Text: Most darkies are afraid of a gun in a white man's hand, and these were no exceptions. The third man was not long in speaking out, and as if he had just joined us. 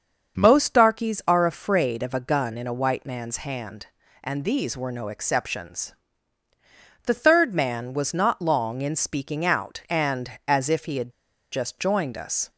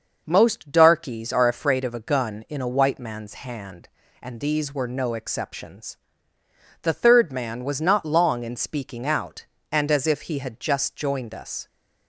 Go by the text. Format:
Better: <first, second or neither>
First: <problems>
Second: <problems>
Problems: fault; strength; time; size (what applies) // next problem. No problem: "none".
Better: second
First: starts louder than the rest; until 1.4 s; 6.5 dB // pauses between "had" and "just"; at 11.1 s; 0.41 s long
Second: starts louder than the rest; noticeable; until 1.2 s; 6 dB